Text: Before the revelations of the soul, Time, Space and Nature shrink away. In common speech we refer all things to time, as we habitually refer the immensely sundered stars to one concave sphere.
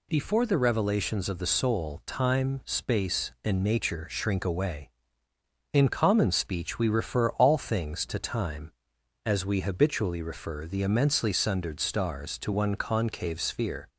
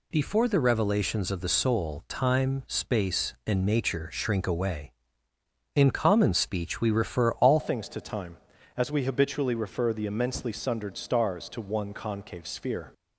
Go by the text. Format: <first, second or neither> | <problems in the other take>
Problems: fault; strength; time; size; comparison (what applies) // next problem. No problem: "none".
first | changes voice at "things"; from 7.5 s on; 5.4 s long